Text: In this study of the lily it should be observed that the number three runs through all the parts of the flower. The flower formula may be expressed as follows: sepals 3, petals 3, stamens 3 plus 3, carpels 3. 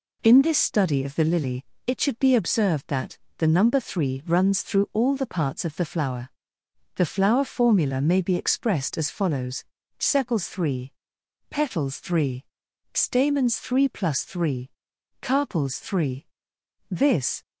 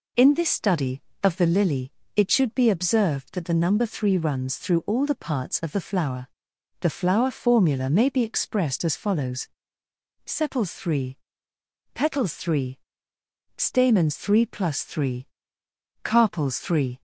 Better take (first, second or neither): second